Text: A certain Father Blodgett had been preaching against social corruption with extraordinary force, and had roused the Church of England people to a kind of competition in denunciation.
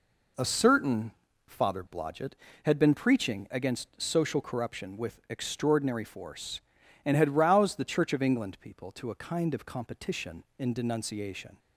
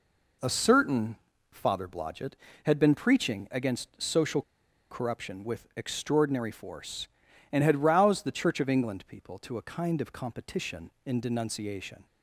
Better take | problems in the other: first | pauses between "certain" and "Father"; slight; at 1.1 s; 0.34 s long; slight in the first // pauses between "social" and "corruption"; noticeable; at 4.4 s; 0.49 s long

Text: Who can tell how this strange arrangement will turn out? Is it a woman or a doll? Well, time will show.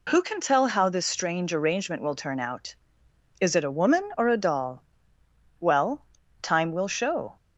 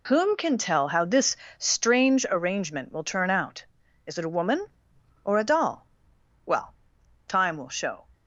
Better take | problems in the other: first | says "Whom" for "Who"; at 0.0 s // pauses between "this" and "strange"; slight; at 1.3 s; 0.24 s long

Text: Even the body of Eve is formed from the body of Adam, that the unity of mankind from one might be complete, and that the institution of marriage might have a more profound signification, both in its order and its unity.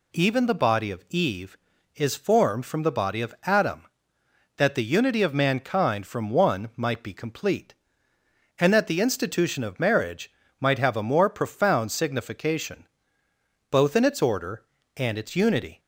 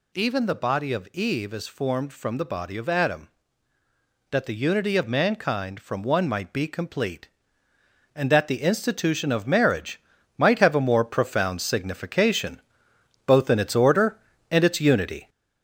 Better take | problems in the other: first | gets louder; noticeable; throughout; 4.5 dB // pauses between "marriage" and "might"; at 9.9 s; 0.38 s long; slight in the first

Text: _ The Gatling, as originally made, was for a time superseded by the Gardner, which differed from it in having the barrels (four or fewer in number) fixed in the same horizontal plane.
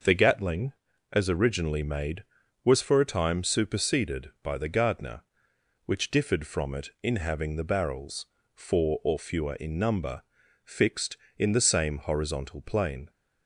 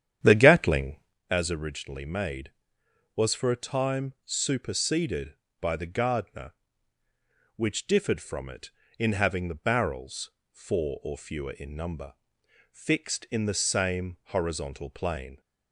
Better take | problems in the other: first | starts louder than the rest; strong; until 1.1 s; 9.5 dB

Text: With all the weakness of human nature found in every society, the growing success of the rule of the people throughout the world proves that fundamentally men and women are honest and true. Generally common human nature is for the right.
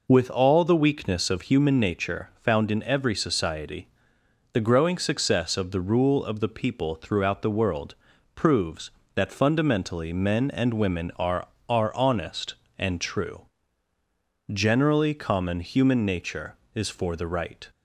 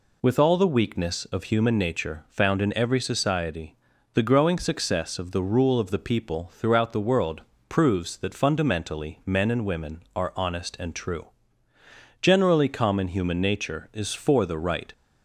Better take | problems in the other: second | pauses between "world" and "proves"; at 7.9 s; 0.42 s long; slight in the second // says "are" twice; at 11.6 s

